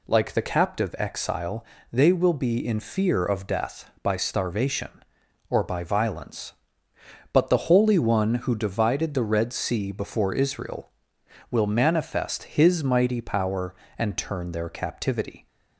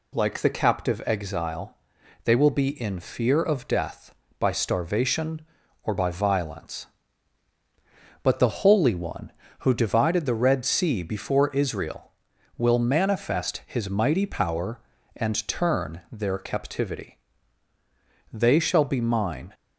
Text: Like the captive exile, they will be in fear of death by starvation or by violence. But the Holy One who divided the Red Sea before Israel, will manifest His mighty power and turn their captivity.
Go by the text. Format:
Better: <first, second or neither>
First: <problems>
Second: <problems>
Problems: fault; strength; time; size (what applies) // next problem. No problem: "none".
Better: first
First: none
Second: goes on to say "They shall be Mine"; noticeable; from 18.3 s on; 1.2 s long